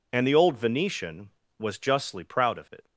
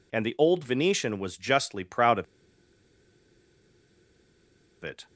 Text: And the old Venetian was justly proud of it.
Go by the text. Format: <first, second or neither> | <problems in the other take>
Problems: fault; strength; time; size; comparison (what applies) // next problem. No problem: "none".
first | pauses between "of" and "it"; strong; at 2.2 s; 2.5 s long